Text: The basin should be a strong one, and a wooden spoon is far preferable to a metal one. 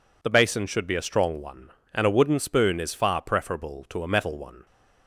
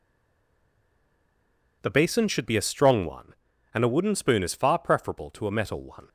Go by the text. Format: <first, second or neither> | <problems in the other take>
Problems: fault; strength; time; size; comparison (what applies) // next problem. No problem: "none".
first | stays silent before the first word; noticeable; until 1.8 s; 1.8 s long